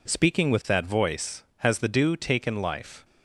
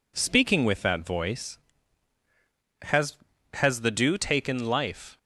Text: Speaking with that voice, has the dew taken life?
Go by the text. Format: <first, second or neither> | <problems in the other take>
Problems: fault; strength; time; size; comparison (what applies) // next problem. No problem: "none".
first | says "has" twice; at 3.5 s